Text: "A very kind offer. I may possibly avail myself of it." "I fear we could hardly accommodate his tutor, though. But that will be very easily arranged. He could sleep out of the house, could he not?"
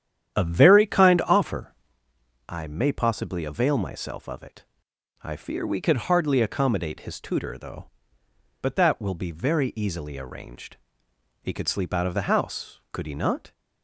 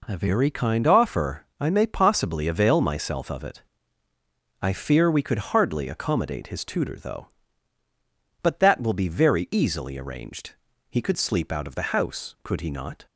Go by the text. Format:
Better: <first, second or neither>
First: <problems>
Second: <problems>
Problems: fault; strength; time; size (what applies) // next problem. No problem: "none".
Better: second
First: starts louder than the rest; strong; until 2.0 s; 10 dB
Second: none